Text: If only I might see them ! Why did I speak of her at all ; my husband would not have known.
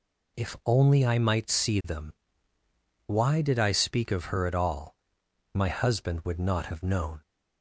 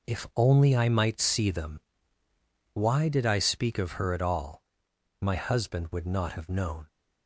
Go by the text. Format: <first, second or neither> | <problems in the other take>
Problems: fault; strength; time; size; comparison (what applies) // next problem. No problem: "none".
first | gets quieter; strong; throughout; 10.5 dB